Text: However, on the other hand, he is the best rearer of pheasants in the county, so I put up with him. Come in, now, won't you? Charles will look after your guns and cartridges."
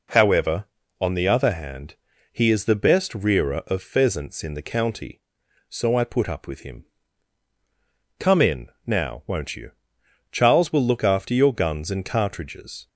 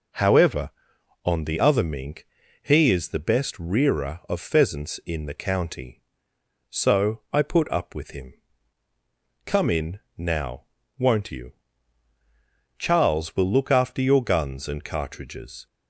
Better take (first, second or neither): first